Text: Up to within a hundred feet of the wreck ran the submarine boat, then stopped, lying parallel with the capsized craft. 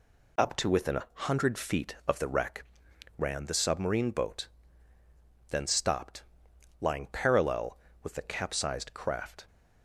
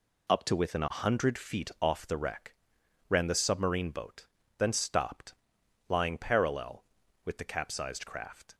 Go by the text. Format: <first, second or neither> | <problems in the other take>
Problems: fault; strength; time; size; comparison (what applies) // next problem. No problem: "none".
first | says "off" for "of"; at 1.8 s // pauses between "wreck" and "ran"; noticeable; at 2.5 s; 0.56 s long; noticeable in the first